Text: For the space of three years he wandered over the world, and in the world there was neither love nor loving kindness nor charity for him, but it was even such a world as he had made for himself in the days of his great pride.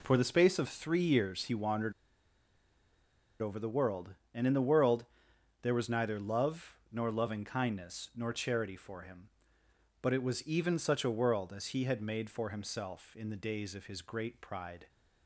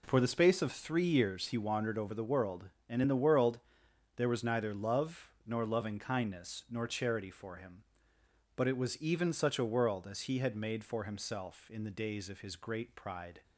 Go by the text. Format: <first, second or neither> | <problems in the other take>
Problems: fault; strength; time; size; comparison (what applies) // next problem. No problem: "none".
second | pauses between "wandered" and "over"; strong; at 1.9 s; 1.4 s long // pauses between "world" and "there"; noticeable; at 5.0 s; 0.56 s long; noticeable in the second // pauses between "love" and "nor"; slight; at 6.7 s; 0.16 s long; slight in the second